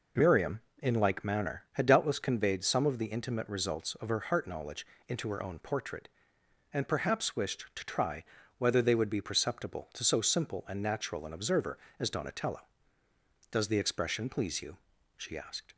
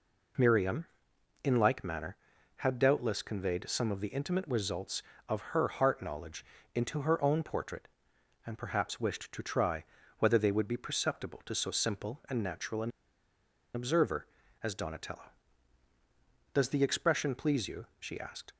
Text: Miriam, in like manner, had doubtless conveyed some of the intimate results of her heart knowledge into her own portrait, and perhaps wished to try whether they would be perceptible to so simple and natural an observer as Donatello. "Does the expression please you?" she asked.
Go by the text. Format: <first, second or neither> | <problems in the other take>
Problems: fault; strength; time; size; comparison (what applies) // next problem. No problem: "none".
first | pauses between "knowledge" and "into"; slight; at 6.4 s; 0.30 s long; slight in the first // pauses between "try" and "whether"; slight; at 9.8 s; 0.34 s long; slight in the first // pauses between "an" and "observer"; noticeable; at 12.8 s; 0.84 s long